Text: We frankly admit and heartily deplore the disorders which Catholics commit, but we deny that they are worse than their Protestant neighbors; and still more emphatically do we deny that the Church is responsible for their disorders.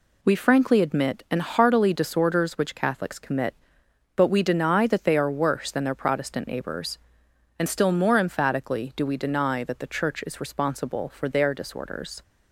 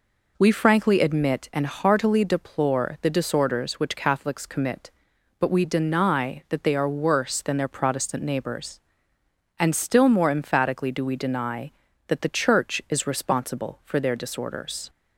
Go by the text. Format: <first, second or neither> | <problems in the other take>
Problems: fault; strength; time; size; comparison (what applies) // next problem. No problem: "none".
second | skips "deplore the"; at 1.9 s